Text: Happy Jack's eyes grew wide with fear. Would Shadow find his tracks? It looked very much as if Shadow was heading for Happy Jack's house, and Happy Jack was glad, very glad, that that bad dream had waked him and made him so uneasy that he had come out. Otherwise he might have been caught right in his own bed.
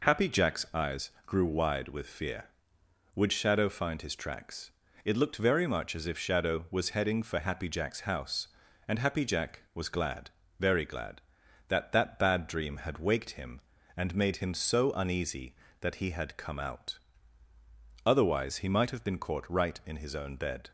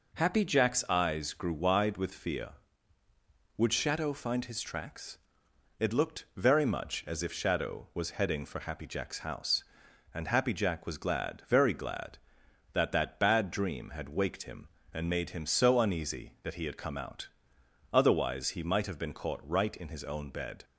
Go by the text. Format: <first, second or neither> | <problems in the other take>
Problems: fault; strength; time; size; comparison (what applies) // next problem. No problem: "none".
neither | none